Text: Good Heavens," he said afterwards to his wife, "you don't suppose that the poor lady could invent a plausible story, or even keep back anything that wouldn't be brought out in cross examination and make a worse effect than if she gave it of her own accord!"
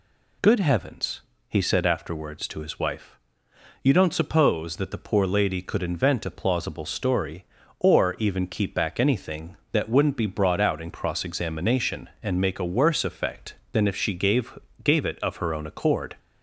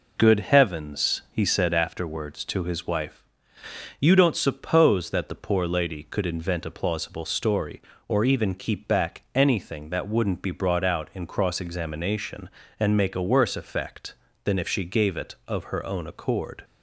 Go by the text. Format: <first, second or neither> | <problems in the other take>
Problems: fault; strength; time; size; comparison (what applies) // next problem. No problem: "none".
second | says "gave" twice; at 14.8 s